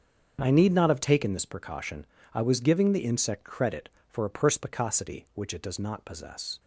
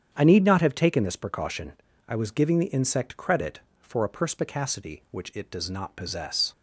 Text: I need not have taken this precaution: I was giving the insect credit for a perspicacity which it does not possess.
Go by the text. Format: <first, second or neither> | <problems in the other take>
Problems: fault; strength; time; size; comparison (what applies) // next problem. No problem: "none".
neither | starts louder than the rest; strong; the same in both